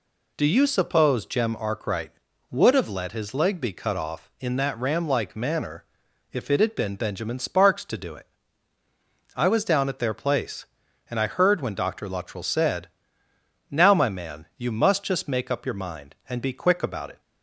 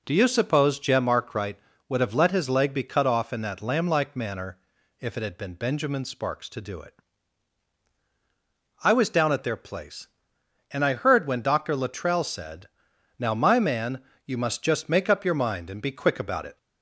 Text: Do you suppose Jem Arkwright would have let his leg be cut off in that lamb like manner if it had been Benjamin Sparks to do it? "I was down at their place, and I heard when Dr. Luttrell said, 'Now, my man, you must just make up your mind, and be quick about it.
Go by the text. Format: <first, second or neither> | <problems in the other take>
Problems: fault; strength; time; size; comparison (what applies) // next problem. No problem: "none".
second | says "ram" for "lamb"; at 4.7 s // pauses between "manner" and "if"; noticeable; at 5.8 s; 0.48 s long; also in the second